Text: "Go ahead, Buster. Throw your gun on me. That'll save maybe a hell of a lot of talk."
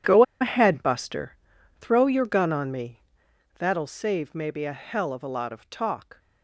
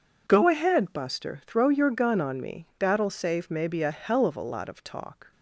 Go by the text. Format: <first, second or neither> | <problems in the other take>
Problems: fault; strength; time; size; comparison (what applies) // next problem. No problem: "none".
second | pauses between "Go" and "ahead"; slight; at 0.2 s; 0.17 s long